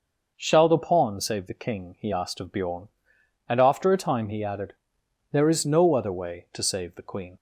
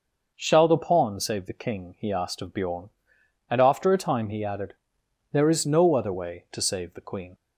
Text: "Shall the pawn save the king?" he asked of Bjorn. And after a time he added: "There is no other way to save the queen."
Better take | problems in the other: neither | none

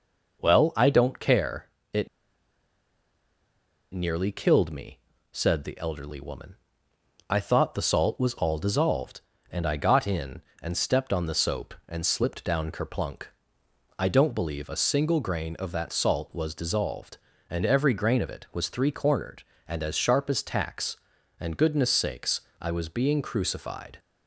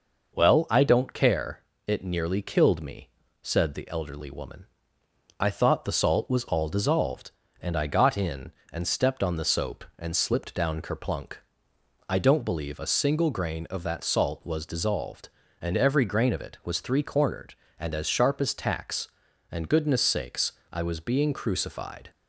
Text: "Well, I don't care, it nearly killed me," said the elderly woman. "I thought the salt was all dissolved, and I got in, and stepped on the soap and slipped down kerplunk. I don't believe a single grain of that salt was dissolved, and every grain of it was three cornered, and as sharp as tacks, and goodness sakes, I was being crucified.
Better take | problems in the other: second | pauses between "it" and "nearly"; strong; at 2.0 s; 1.8 s long

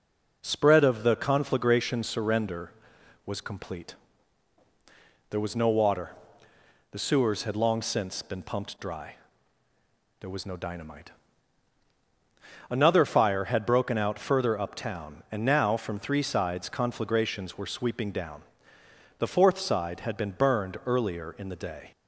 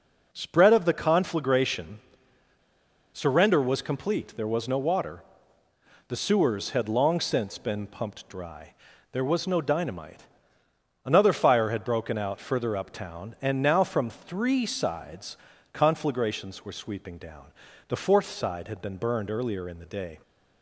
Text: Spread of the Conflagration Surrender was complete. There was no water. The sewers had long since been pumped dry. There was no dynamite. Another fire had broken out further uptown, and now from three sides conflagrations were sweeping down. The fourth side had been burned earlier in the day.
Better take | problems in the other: first | pauses between "Conflagration" and "Surrender"; at 1.9 s; 1.1 s long // pauses between "sides" and "conflagrations"; slight; at 15.3 s; 0.34 s long

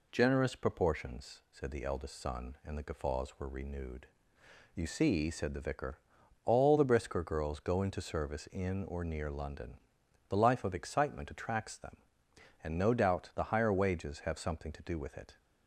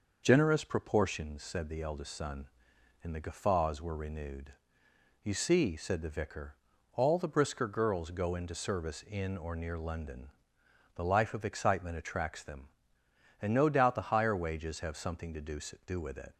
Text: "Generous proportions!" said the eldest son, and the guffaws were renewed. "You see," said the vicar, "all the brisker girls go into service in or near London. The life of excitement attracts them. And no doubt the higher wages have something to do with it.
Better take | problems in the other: first | says "do" twice; at 15.8 s

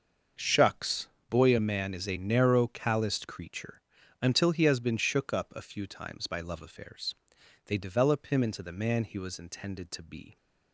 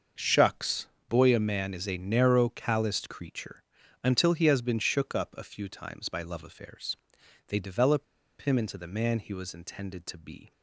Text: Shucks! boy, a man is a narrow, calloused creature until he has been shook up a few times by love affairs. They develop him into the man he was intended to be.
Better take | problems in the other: first | starts louder than the rest; until 1.4 s; 6.5 dB; also in the first // pauses between "creature" and "until"; at 3.6 s; 0.40 s long; also in the first // pauses between "develop" and "him"; slight; at 8.0 s; 0.35 s long

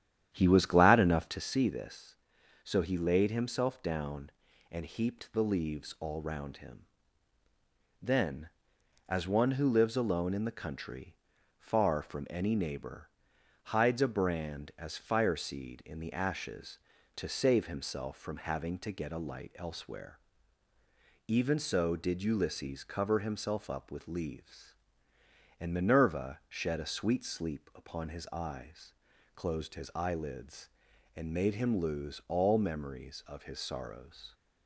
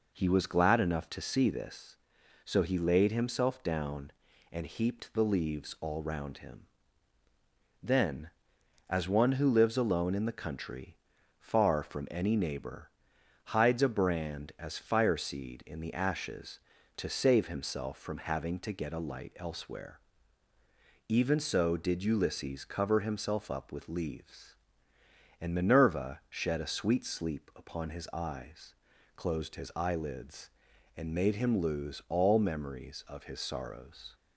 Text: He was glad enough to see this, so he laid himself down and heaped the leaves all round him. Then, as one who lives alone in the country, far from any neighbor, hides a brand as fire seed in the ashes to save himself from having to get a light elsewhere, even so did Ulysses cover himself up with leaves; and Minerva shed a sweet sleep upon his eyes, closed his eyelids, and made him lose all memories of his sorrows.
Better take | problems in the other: second | starts louder than the rest; strong; until 1.5 s; 10.5 dB

